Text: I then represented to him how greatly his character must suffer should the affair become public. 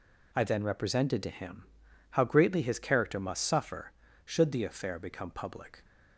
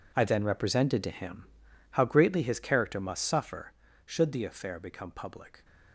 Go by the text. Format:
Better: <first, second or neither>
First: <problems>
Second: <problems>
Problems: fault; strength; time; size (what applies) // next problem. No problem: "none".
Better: first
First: pauses between "him" and "how"; at 1.6 s; 0.44 s long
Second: gets quieter; strong; throughout; 14.5 dB // pauses between "him" and "how"; at 1.4 s; 0.44 s long